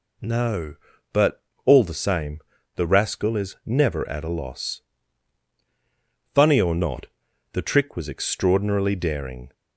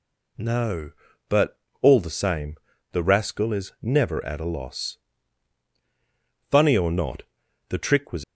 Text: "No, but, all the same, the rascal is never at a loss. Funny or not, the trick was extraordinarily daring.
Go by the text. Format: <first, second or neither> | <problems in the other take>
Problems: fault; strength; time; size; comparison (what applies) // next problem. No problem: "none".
first | stops before "extraordinarily daring"; at 8.2 s